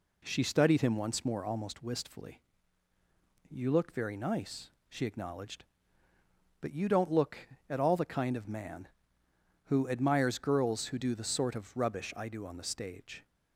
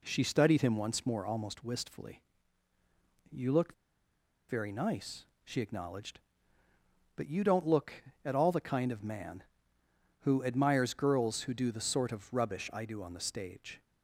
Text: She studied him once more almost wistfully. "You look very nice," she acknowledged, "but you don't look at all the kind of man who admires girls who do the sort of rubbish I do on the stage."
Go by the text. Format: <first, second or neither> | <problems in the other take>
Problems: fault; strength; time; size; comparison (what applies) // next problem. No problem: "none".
first | pauses between "look" and "very"; noticeable; at 3.7 s; 0.75 s long